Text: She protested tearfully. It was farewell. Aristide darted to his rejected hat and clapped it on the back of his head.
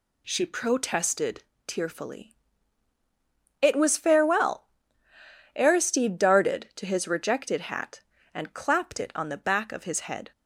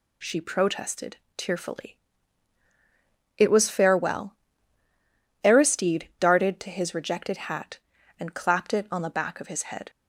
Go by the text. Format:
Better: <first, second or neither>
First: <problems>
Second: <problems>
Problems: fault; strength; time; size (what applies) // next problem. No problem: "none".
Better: neither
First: pauses between "protested" and "tearfully"; slight; at 1.4 s; 0.24 s long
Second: pauses between "protested" and "tearfully"; slight; at 1.1 s; 0.20 s long